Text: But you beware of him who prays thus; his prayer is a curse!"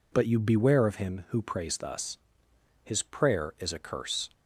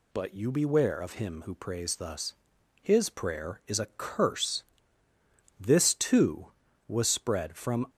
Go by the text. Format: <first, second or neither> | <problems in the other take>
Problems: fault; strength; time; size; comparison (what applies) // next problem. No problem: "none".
first | goes on to say "This too was spread from"; strong; from 5.5 s on; 2.2 s long